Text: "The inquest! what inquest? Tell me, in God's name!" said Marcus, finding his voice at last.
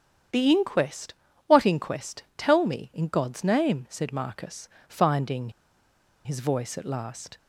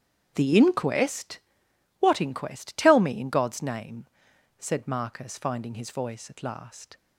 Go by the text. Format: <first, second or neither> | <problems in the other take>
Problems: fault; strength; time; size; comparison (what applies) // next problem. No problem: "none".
second | starts louder than the rest; strong; until 1.6 s; 8.5 dB; strong in the second // pauses between "finding" and "his"; noticeable; at 5.5 s; 0.74 s long